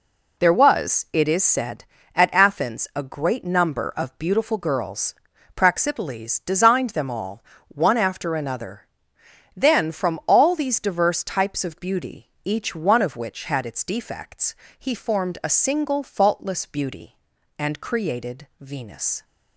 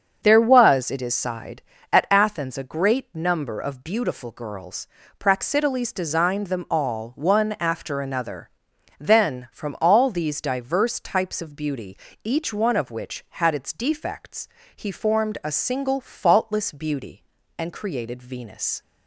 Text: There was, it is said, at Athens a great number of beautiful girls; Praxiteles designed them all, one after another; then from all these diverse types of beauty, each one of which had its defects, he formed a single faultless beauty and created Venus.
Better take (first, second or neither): first